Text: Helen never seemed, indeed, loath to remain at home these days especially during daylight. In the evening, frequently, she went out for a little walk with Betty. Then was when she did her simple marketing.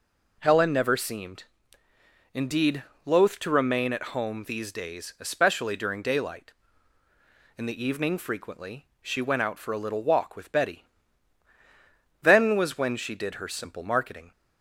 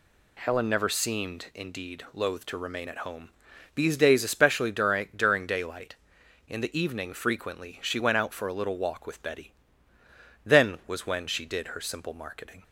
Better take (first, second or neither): first